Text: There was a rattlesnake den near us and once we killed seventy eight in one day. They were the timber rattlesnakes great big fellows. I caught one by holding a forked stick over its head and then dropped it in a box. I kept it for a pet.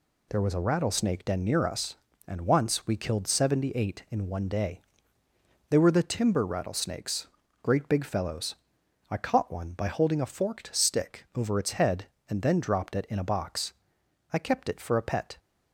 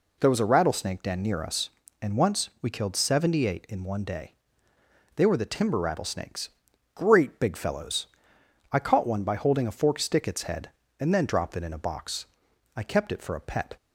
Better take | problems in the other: first | pauses between "rattlesnakes" and "great"; noticeable; at 6.4 s; 0.48 s long; slight in the first // skips "over"; at 10.2 s

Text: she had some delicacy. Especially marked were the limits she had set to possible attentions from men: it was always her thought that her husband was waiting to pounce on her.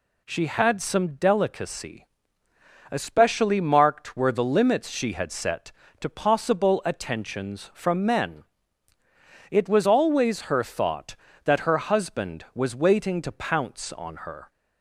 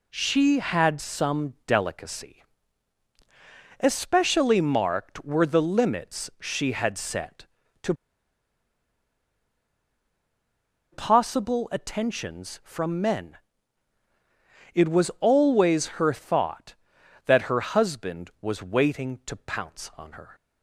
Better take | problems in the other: first | pauses between "to" and "possible"; strong; at 7.9 s; 2.9 s long

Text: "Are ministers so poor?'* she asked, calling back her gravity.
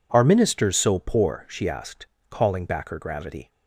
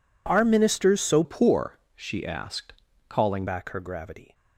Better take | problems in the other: first | changes voice from "poor" to "calling"; from 1.2 to 3.4 s; 2.2 s long

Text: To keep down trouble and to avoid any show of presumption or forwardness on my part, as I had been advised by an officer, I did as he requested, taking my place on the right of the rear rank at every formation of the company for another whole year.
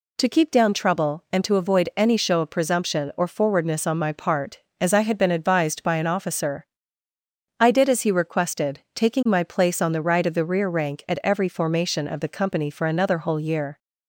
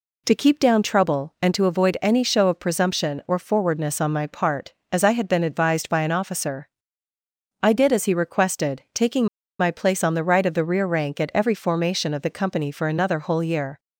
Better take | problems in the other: first | pauses between "taking" and "my"; slight; at 9.2 s; 0.33 s long

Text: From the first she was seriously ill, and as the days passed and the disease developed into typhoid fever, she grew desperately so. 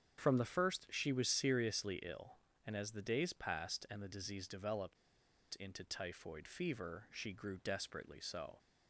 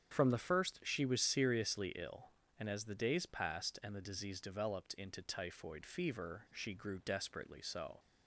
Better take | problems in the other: second | starts louder than the rest; strong; until 1.2 s; 7.5 dB; strong in the second // pauses between "developed" and "into"; noticeable; at 4.9 s; 0.63 s long

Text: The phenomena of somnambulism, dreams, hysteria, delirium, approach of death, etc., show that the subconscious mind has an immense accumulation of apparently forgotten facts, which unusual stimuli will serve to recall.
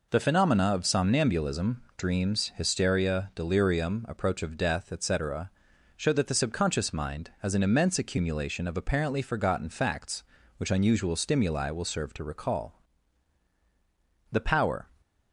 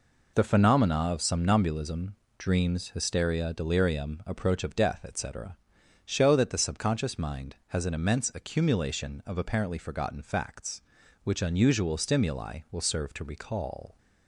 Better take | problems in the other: second | goes on to say "The power"; from 14.3 s on; 0.56 s long

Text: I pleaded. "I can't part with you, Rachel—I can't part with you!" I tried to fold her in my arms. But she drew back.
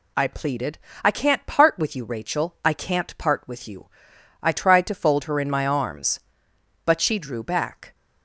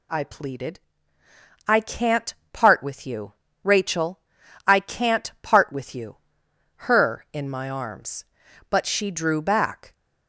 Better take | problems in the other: first | pauses between "can't" and "part"; slight; at 2.3 s; 0.18 s long // skips "I tried to fold"; at 6.5 s

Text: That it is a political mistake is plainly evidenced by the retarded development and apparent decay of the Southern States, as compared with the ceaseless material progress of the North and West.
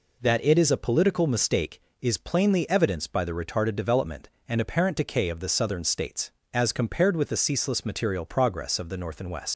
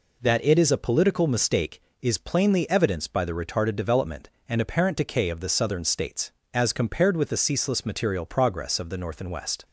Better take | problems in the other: second | leaves "West" unfinished; at 9.5 s; 105 ms

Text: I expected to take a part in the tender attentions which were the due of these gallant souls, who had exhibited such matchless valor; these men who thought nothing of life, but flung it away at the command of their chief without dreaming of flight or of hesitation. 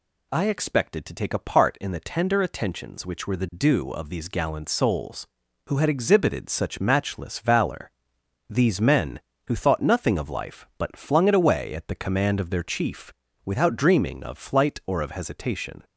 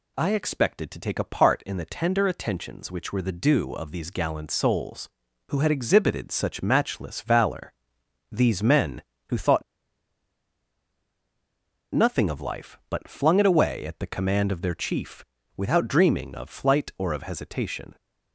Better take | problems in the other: first | pauses between "thought" and "nothing"; strong; at 9.6 s; 2.3 s long // pauses between "chief" and "without"; slight; at 15.2 s; 0.32 s long; slight in the first

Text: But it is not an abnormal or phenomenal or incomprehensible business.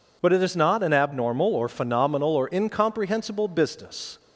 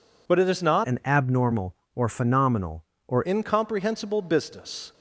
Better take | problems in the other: first | changes voice from "an" to "or"; from 0.8 to 3.2 s; 2.4 s long

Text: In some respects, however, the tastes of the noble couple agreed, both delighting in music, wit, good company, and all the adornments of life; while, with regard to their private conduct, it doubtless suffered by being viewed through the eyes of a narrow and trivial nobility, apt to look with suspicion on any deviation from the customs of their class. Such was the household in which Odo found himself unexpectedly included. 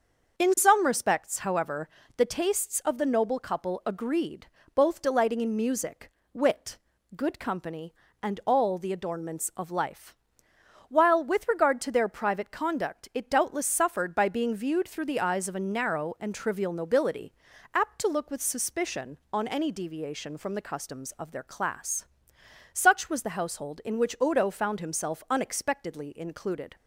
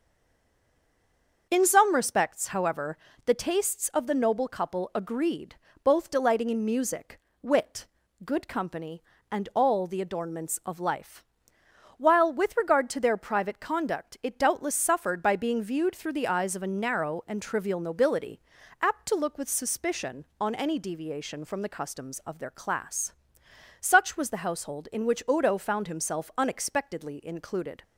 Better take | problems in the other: first | stays silent before the first word; noticeable; until 1.4 s; 1.4 s long // starts louder than the rest; until 2.5 s; 6.5 dB; also in the first

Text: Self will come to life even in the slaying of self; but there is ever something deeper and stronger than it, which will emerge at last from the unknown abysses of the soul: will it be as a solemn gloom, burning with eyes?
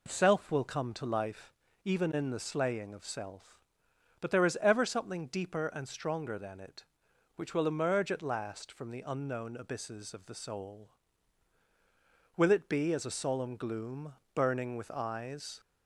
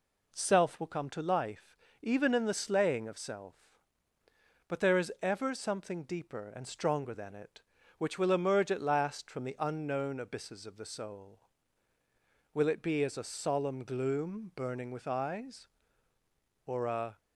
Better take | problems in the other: first | pauses between "life" and "even"; slight; at 1.7 s; 0.26 s long; slight in the first // goes on to say "or a"; from 16.6 s on; 0.54 s long

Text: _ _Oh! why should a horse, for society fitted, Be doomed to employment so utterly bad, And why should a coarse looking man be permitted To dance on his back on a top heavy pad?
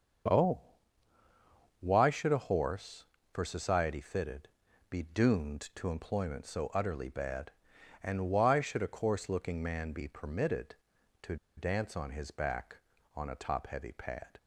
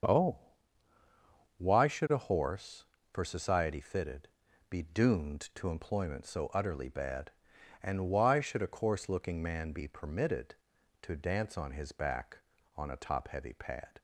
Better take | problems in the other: second | starts louder than the rest; until 2.4 s; 6.5 dB; also in the second // pauses between "To" and "dance"; slight; at 11.3 s; 0.20 s long

